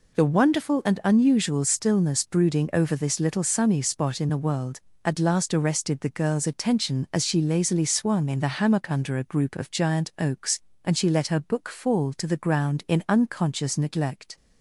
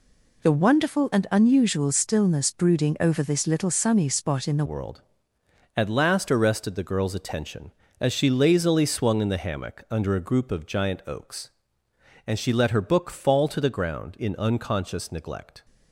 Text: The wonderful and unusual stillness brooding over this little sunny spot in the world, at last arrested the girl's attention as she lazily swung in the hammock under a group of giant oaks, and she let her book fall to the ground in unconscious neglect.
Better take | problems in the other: first | changes voice at "world"; from 4.6 s on; 11.0 s long

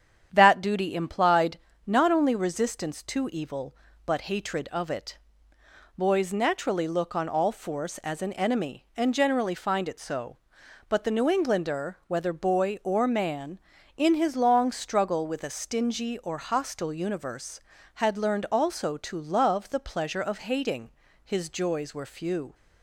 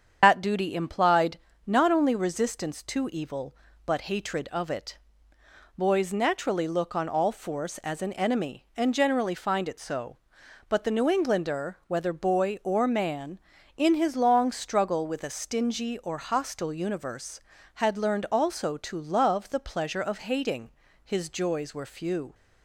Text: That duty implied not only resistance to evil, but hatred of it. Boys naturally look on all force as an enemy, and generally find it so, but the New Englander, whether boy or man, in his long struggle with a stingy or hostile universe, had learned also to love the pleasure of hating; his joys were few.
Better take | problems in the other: first | loses the start of "That"; at 0.2 s; 105 ms // starts louder than the rest; strong; until 1.2 s; 7.5 dB; strong in the first // pauses between "implied" and "not"; slight; at 1.3 s; 0.28 s long; slight in the first

